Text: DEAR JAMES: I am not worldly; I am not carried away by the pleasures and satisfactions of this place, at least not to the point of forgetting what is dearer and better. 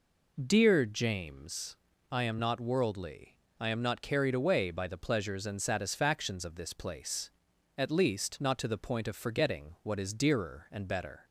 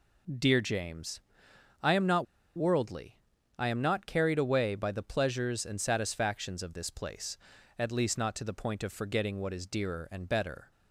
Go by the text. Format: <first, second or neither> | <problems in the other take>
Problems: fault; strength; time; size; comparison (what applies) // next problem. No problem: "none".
first | pauses between "not" and "worldly"; slight; at 2.2 s; 0.31 s long